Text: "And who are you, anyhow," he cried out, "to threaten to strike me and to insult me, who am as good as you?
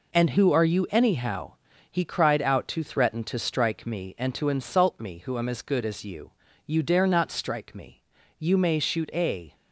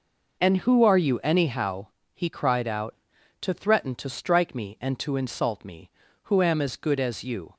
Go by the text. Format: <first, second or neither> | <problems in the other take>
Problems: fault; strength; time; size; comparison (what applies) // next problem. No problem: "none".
second | goes on to say "You dare not strike me You may shoot a"; strong; from 6.6 s on; 2.8 s long